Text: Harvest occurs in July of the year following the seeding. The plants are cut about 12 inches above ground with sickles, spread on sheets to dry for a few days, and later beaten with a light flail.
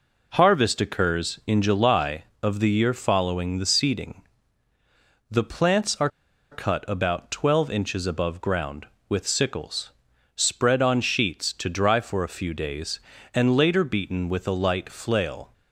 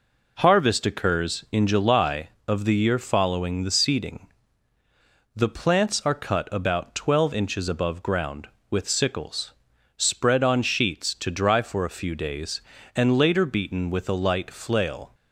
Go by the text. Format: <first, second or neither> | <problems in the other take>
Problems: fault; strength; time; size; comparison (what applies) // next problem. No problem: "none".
second | pauses between "are" and "cut"; at 6.0 s; 0.43 s long